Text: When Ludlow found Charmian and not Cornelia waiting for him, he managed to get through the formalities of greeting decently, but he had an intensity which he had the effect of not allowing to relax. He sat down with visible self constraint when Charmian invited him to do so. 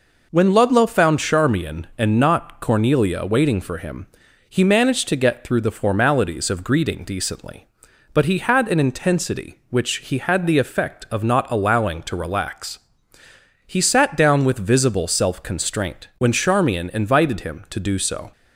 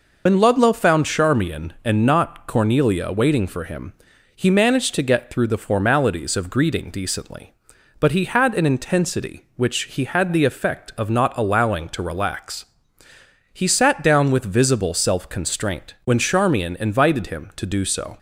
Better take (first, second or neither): first